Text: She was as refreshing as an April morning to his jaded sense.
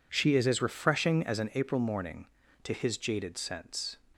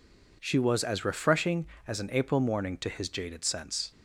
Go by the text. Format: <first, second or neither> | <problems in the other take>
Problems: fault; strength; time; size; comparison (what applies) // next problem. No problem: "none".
second | says "is" for "was"; at 0.3 s